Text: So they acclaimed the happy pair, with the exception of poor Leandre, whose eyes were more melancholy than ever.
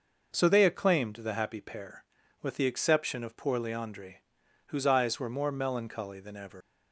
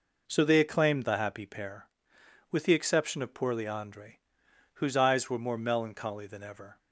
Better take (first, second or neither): second